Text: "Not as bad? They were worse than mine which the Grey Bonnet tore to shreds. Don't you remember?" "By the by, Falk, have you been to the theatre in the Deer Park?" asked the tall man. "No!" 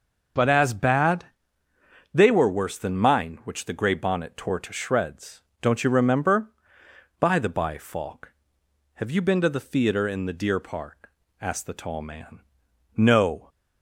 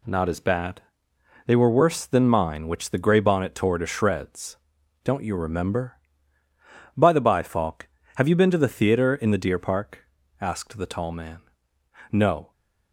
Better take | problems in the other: second | starts louder than the rest; until 2.2 s; 6.5 dB // says "But" for "Not"; at 0.3 s

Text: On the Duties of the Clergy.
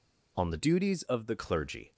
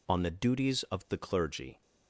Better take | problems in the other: second | changes voice from "Duties" to "the"; from 0.5 to 1.3 s; 0.8 s long

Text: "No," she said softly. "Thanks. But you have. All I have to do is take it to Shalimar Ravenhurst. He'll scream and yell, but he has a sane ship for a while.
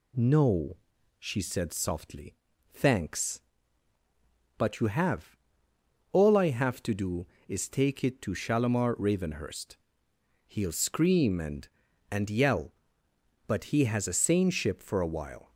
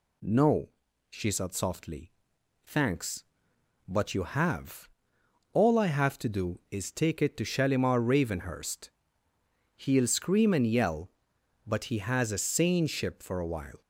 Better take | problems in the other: second | says "and" twice; at 12.0 s

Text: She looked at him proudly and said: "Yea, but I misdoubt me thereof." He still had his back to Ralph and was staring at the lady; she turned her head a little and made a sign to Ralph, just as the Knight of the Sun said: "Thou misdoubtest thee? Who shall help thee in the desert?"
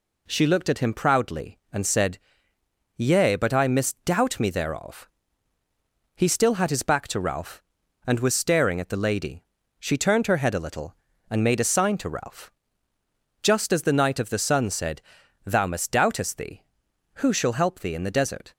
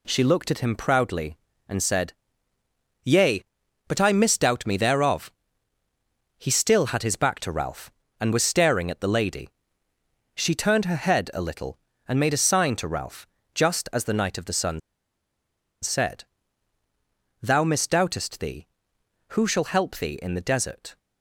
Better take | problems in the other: first | pauses between "Sun" and "said"; at 14.8 s; 1.0 s long

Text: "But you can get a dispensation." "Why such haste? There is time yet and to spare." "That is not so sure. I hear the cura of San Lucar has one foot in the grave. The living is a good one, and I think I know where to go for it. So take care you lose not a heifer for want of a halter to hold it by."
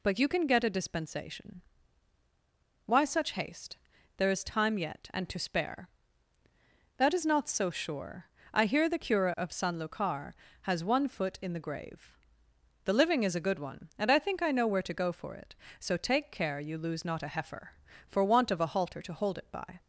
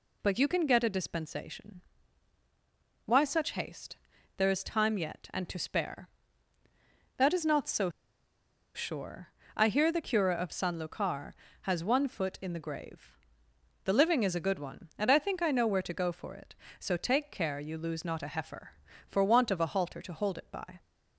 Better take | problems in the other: first | pauses between "so" and "sure"; noticeable; at 7.8 s; 0.85 s long

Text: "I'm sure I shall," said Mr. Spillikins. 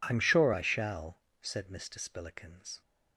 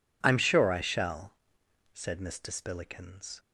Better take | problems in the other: neither | none

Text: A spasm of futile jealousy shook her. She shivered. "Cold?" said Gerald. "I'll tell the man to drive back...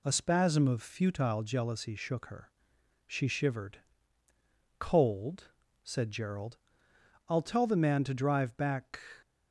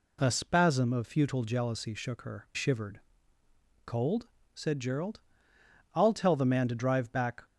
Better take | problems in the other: first | skips "She"; at 2.5 s

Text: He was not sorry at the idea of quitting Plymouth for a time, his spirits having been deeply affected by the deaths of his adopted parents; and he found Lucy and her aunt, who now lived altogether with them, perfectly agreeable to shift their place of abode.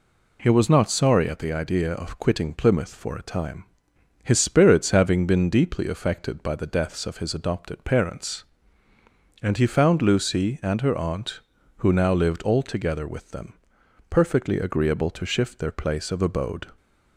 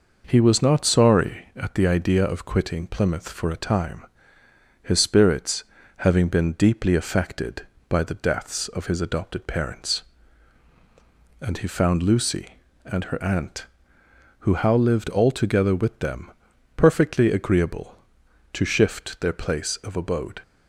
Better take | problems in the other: first | pauses between "spirits" and "having"; slight; at 5.6 s; 0.32 s long // says "how" for "now"; at 14.5 s

